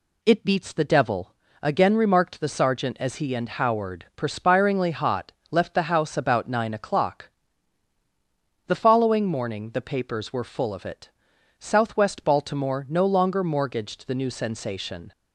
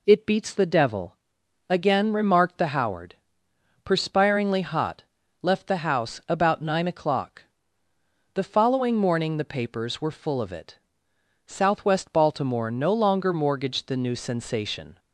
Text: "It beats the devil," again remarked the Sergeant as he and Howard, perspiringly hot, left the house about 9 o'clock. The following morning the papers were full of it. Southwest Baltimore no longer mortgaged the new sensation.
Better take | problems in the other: first | skips "Sergeant as he and"; at 2.7 s

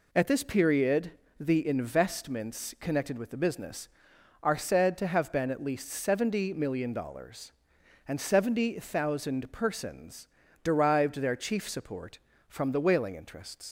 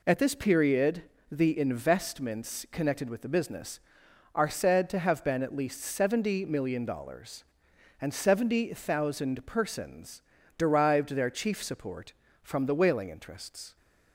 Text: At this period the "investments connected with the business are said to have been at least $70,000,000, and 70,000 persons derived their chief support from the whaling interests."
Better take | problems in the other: second | pauses between "period" and "the"; slight; at 1.1 s; 0.28 s long; slight in the second // pauses between "persons" and "derived"; at 10.2 s; 0.38 s long; also in the second // leaves "interests" unfinished; at 13.6 s; 105 ms

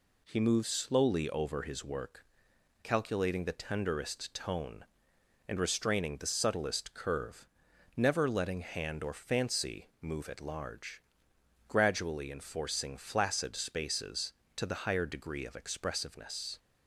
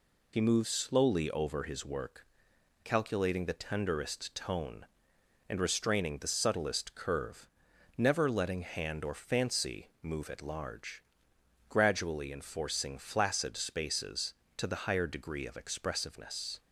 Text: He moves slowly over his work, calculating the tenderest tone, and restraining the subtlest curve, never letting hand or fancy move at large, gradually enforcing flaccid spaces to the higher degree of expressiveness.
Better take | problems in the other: first | loses the start of "He"; at 0.3 s; 75 ms

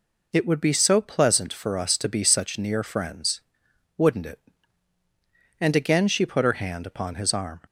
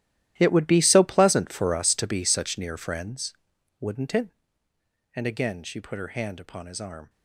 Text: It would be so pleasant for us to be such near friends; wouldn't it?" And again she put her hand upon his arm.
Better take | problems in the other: first | gets quieter; strong; throughout; 16 dB

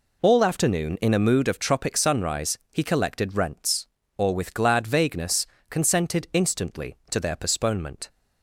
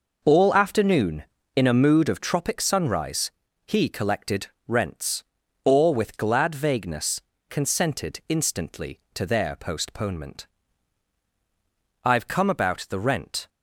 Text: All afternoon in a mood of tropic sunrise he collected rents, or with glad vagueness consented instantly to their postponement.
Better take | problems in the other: first | pauses between "sunrise" and "he"; slight; at 3.3 s; 0.34 s long; slight in the first // pauses between "collected" and "rents"; slight; at 4.4 s; 0.22 s long // pauses between "vagueness" and "consented"; slight; at 7.2 s; 0.30 s long; slight in the first // goes on to say "I've come about the rent"; from 12.0 s on; 1.4 s long

